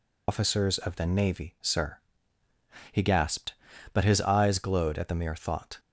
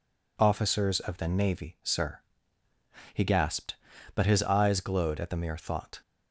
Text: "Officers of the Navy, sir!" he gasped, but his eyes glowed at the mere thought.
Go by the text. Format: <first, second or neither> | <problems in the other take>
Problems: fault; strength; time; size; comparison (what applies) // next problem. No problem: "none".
second | loses the start of "Officers"; at 0.2 s; 110 ms